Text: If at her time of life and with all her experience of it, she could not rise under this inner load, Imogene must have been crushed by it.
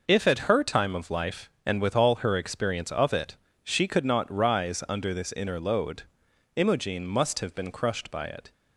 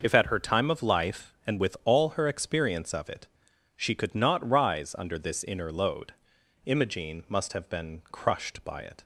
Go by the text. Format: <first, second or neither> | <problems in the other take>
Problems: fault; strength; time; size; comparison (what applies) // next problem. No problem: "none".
neither | none